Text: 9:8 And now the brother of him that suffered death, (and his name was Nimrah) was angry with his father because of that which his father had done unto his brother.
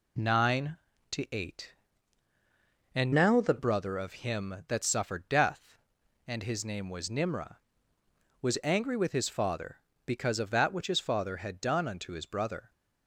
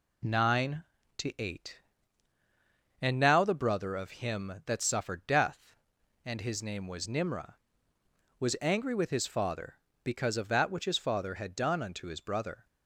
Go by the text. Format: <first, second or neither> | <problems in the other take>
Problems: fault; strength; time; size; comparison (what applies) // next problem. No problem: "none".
second | changes voice from "now" to "the"; from 3.1 to 3.5 s; 0.4 s long